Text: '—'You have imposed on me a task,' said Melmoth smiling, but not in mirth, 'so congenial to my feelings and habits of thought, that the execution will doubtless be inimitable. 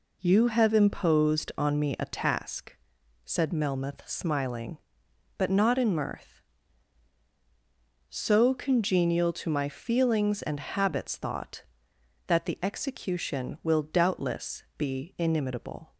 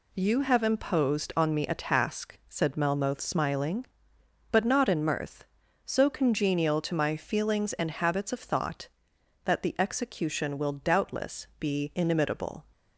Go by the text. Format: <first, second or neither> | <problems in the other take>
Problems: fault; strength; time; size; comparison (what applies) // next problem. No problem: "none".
second | skips "of"; at 11.1 s